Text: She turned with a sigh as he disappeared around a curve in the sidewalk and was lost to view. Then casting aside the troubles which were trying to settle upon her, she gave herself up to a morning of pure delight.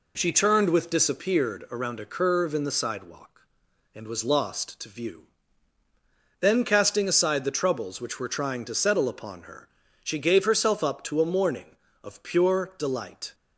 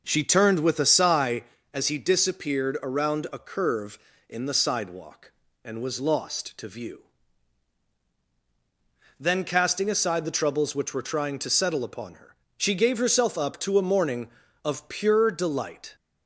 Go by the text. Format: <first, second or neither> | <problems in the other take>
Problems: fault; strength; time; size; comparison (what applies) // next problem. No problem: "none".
second | skips "a sigh as he"; at 0.8 s